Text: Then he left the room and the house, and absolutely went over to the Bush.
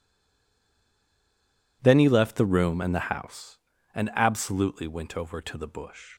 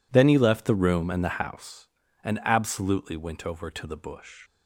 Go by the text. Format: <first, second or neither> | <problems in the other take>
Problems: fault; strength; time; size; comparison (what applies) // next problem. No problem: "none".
second | stays silent before the first word; noticeable; until 1.8 s; 1.8 s long